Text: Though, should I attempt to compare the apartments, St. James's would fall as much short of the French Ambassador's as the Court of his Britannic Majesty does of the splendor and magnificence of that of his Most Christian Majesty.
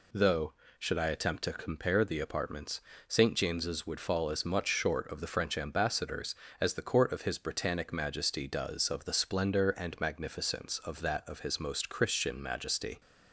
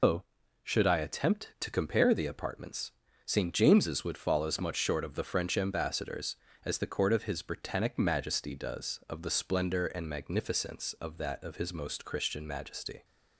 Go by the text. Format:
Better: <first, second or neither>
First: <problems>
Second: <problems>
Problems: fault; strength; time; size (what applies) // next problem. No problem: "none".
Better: first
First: none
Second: loses the start of "Though"; at 0.0 s; 135 ms